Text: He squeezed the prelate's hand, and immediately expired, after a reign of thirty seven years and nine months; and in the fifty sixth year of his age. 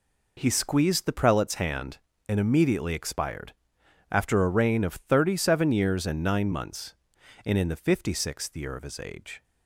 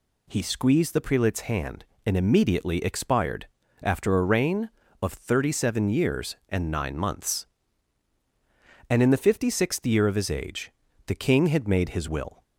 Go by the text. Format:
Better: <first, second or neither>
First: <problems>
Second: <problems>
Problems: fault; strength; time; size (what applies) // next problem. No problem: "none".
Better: first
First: none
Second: goes on to say "The king had made his will"; from 11.0 s on; 1.3 s long